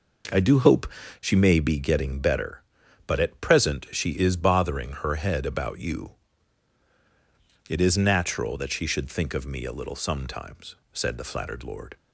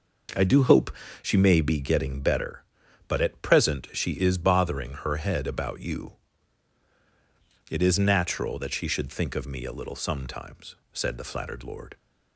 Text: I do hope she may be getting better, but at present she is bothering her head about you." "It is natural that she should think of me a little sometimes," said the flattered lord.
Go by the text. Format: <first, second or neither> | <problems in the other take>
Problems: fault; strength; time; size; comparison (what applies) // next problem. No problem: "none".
neither | pauses between "hope" and "she"; slight; the same in both